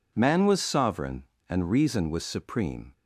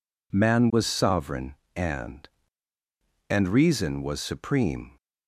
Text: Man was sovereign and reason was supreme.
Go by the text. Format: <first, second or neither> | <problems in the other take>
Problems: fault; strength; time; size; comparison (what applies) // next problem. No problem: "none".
first | says "and" twice; at 3.2 s